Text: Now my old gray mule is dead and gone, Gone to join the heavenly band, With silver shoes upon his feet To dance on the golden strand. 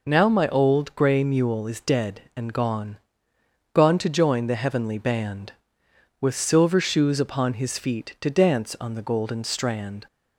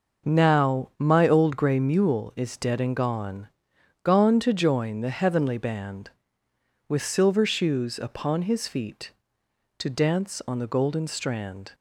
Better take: neither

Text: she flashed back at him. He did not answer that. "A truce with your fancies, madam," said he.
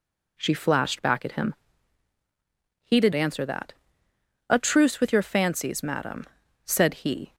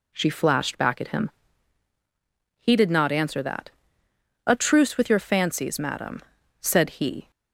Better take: second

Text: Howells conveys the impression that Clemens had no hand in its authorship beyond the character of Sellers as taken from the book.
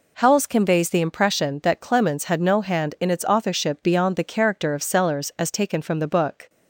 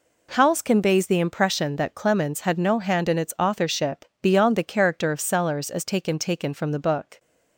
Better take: first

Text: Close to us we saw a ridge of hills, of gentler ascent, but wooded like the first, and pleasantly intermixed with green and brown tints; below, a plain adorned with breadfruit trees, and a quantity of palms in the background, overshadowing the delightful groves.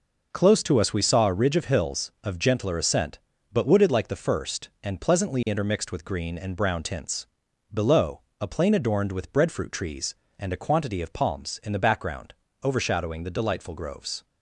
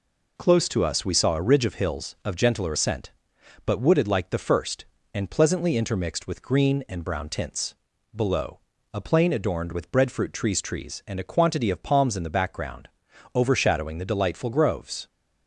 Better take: first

